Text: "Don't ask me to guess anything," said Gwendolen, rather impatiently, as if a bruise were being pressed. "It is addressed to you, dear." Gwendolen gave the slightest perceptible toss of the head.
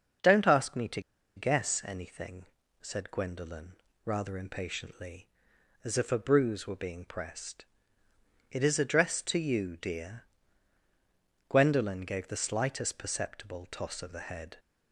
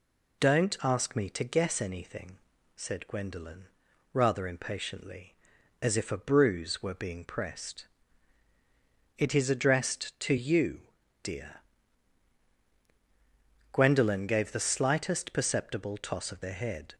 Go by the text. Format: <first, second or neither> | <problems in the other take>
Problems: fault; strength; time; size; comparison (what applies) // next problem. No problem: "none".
second | starts louder than the rest; until 1.6 s; 6.5 dB // pauses between "to" and "guess"; at 0.9 s; 0.36 s long